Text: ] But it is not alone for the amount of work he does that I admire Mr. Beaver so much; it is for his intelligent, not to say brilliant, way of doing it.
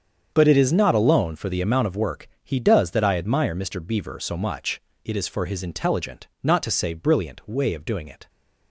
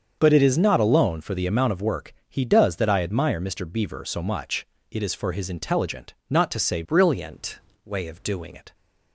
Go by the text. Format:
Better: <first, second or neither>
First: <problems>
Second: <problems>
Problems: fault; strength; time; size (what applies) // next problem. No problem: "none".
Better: first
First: starts louder than the rest; strong; until 1.3 s; 7.5 dB // pauses between "work" and "he"; slight; at 2.2 s; 0.16 s long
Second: starts louder than the rest; until 1.1 s; 7 dB // pauses between "work" and "he"; slight; at 2.1 s; 0.16 s long // changes voice from "brilliant" to "doing"; from 6.8 to 8.5 s; 1.7 s long